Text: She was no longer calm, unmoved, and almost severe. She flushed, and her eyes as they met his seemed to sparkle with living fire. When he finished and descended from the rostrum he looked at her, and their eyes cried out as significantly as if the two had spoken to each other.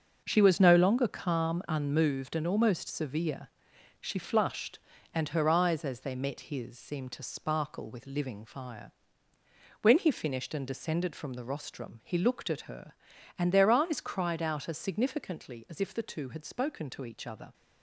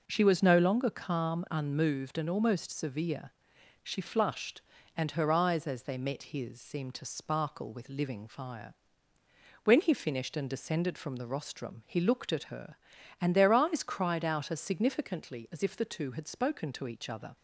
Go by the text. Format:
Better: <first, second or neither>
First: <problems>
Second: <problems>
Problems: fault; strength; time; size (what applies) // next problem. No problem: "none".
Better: second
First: gets quieter; strong; throughout; 9 dB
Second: none